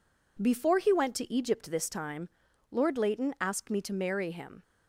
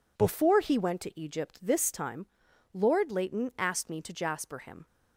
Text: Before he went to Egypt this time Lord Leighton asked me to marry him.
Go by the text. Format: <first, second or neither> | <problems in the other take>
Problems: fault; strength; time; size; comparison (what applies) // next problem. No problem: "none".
first | pauses between "time" and "Lord"; noticeable; at 2.2 s; 0.46 s long; also in the first // says "jasper" for "marry"; at 4.1 s